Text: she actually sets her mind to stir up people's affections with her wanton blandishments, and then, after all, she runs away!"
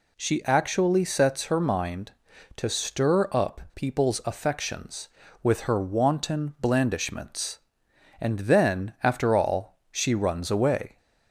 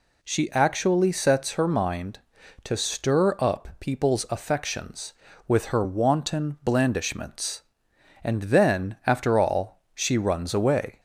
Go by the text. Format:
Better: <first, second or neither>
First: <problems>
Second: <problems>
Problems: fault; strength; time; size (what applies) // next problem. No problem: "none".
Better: neither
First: none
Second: none